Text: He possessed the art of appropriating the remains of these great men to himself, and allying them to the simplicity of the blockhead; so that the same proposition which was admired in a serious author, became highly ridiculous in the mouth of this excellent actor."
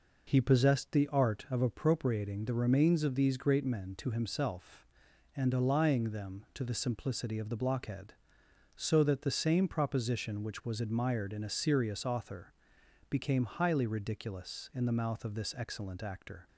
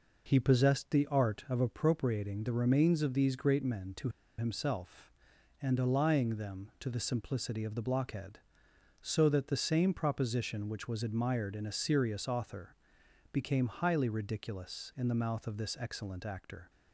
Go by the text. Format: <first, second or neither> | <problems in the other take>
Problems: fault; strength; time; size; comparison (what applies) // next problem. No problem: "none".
first | pauses between "to" and "himself"; slight; at 4.0 s; 0.29 s long